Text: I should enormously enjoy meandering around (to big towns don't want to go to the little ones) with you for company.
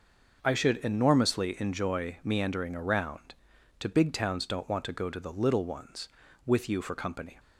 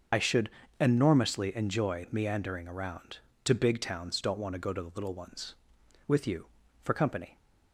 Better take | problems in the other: first | loses the start of "I"; at 0.1 s; 45 ms // starts louder than the rest; until 1.4 s; 6.5 dB; noticeable in the first // pauses between "should" and "enormously"; slight; at 0.4 s; 0.30 s long

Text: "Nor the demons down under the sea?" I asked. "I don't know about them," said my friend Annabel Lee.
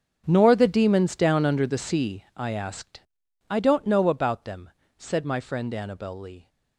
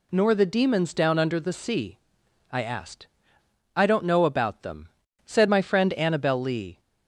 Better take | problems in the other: second | gets quieter; strong; throughout; 16 dB

